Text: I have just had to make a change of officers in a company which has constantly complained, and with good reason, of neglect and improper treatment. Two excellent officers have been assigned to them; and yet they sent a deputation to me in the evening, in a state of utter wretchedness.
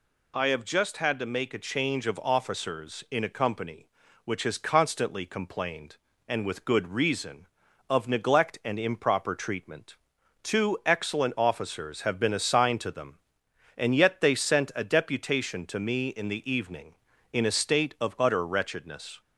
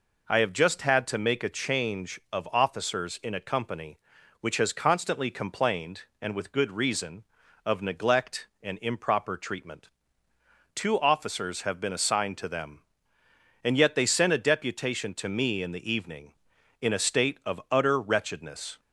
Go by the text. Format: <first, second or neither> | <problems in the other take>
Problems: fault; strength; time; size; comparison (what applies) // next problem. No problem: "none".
first | skips "excellent"; at 10.9 s